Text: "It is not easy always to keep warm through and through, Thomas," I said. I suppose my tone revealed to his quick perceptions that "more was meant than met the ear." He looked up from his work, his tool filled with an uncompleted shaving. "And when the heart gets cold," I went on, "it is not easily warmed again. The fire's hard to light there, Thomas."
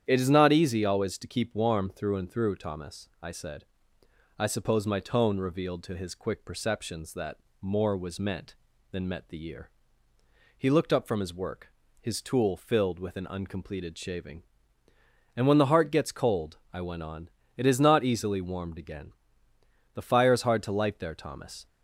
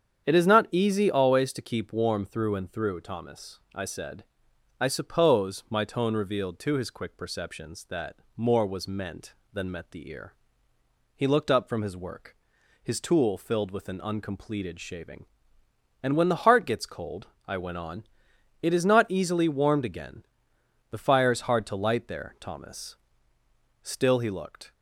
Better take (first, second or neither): first